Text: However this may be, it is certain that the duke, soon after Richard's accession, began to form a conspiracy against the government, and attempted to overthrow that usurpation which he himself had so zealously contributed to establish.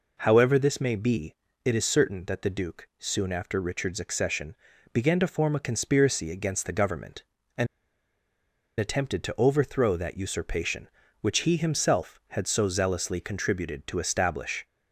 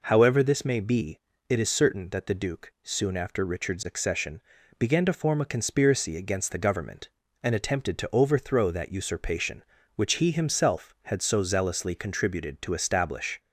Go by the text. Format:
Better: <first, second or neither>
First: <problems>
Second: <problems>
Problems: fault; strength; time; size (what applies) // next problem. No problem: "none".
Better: second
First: pauses between "and" and "attempted"; at 7.6 s; 1.1 s long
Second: none